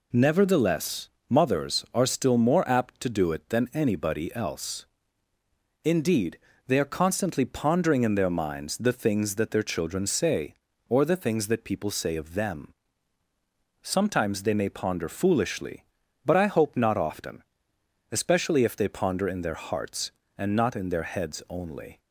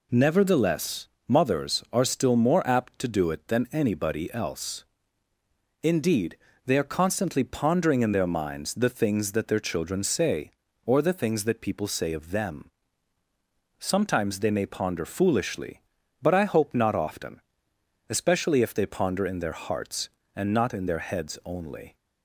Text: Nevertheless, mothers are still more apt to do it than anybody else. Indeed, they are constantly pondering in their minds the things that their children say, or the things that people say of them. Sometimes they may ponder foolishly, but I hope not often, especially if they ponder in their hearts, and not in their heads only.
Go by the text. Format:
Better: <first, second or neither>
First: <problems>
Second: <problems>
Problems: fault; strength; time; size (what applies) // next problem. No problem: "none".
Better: neither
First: none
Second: none